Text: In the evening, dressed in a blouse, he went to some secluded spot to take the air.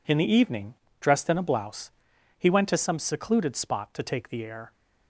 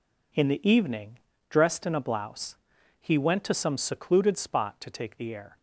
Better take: neither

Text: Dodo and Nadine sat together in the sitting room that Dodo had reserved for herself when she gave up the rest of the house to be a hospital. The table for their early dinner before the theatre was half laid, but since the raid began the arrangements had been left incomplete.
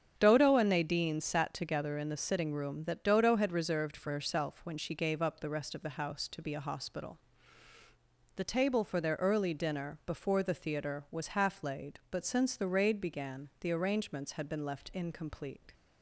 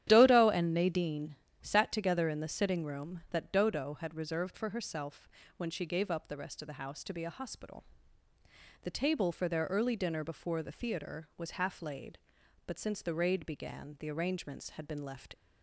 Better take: first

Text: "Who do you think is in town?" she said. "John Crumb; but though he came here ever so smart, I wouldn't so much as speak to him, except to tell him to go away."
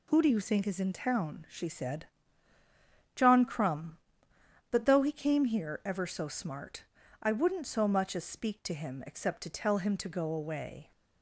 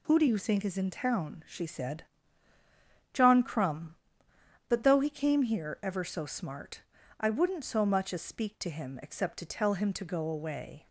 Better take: neither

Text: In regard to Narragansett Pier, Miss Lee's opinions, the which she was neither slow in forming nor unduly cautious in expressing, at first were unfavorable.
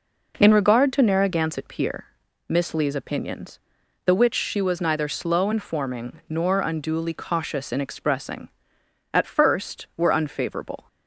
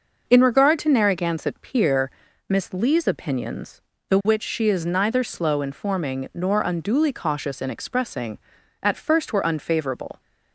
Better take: first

